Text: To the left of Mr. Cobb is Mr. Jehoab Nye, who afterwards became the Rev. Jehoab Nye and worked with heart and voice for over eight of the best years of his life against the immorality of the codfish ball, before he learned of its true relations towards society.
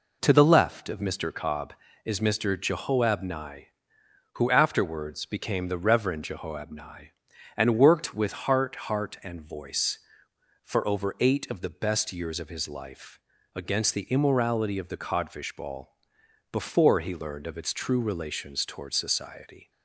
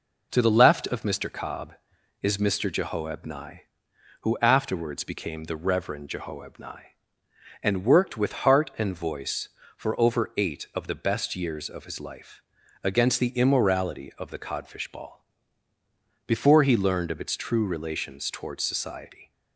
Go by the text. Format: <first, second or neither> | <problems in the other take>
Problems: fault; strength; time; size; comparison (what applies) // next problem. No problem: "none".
second | says "heart" twice; at 8.7 s // pauses between "life" and "against"; at 13.1 s; 0.36 s long; also in the second